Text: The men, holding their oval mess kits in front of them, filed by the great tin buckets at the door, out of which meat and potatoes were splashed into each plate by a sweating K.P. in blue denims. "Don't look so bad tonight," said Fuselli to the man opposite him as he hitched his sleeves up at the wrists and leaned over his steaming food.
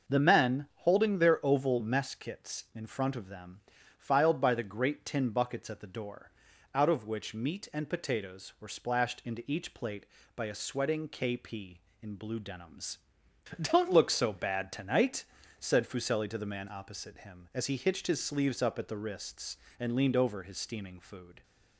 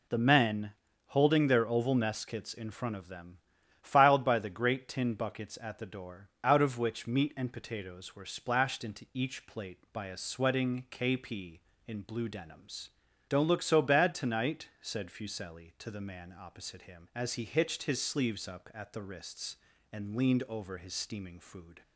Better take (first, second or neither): neither